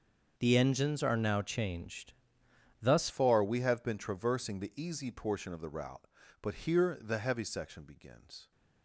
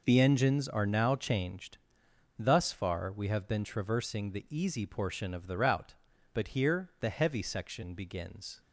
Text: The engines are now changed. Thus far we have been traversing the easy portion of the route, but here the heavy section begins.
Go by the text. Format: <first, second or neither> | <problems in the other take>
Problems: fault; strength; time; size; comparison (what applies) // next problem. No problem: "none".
second | starts louder than the rest; until 1.3 s; 6.5 dB // changes voice at "far"; from 3.0 s on; 5.5 s long